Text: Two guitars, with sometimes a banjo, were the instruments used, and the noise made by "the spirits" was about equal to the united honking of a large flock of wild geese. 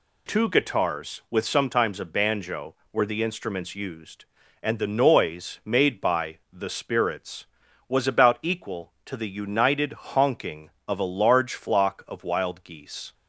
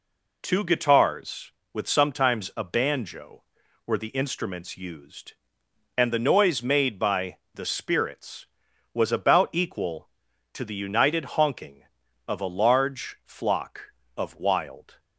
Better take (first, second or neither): first